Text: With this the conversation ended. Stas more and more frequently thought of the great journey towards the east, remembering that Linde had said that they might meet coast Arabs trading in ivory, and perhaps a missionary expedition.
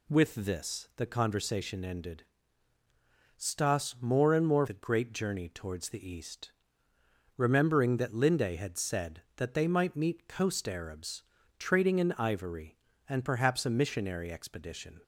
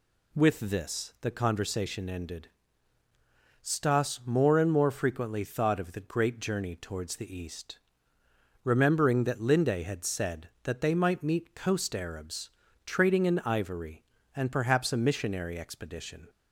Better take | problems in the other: second | skips "frequently thought of"; at 4.6 s // pauses between "Arabs" and "trading"; at 11.2 s; 0.38 s long; also in the second

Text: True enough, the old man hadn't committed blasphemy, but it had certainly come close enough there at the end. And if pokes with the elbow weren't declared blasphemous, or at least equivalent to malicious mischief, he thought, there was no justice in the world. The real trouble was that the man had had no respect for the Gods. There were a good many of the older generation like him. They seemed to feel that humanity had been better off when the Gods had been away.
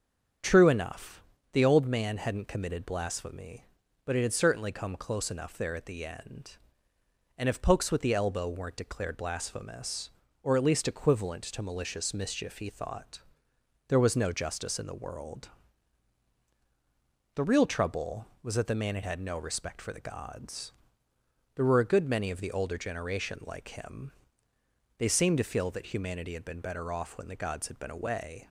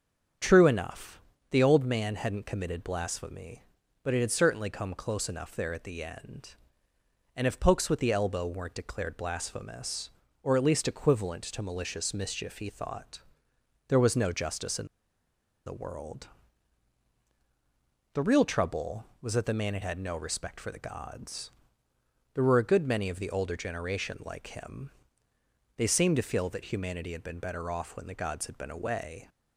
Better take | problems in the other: first | starts louder than the rest; until 1.7 s; 7 dB; also in the first // pauses between "in" and "the"; noticeable; at 14.8 s; 0.80 s long

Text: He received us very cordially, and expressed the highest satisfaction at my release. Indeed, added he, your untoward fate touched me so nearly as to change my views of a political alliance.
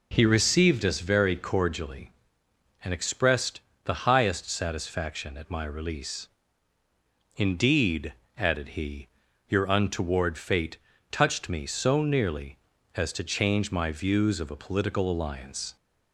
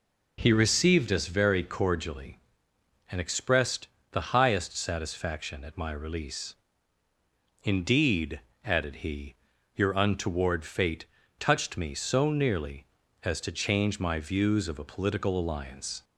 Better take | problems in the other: neither | pauses between "expressed" and "the"; slight; the same in both // pauses between "fate" and "touched"; slight; the same in both

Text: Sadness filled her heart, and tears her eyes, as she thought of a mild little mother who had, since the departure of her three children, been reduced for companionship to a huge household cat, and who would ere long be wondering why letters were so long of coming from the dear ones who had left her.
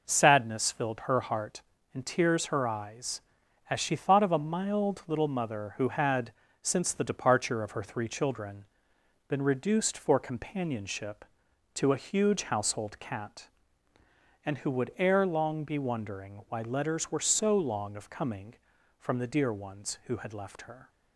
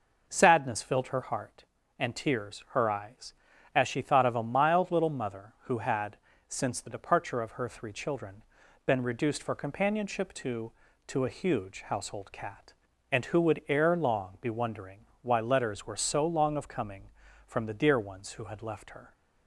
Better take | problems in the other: first | says "to" twice; at 11.0 s // pauses between "wondering" and "why"; slight; at 15.0 s; 0.18 s long

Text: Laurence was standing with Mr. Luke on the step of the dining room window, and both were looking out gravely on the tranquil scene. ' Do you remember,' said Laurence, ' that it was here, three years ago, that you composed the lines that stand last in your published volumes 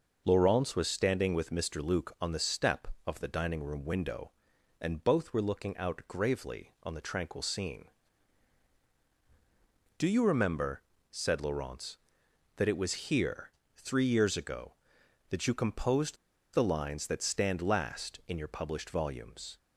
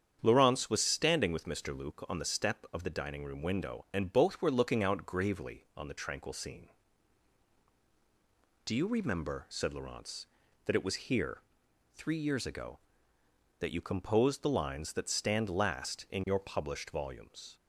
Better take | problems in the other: second | starts louder than the rest; strong; until 1.2 s; 8 dB; strong in the second // pauses between "composed" and "the"; at 16.1 s; 0.37 s long

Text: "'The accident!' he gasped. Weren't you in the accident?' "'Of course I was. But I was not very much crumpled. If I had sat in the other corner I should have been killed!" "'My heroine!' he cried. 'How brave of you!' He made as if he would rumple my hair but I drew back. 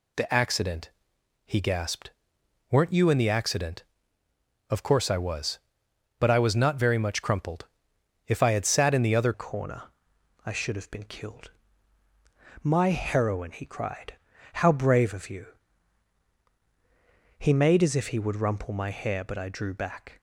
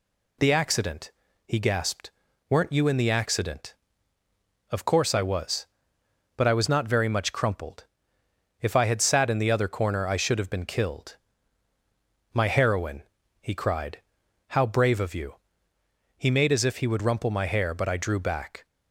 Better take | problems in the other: second | changes voice at "corner"; from 9.3 s on; 10.8 s long // pauses between "corner" and "I"; noticeable; at 9.8 s; 0.62 s long

